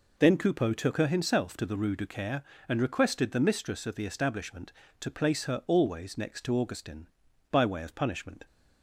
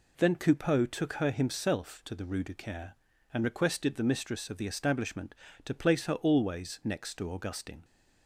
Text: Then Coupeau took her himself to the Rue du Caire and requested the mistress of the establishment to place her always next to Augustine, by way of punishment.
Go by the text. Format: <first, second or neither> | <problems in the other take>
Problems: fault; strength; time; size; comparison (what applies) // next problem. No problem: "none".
first | stops before "by way of punishment"; at 7.8 s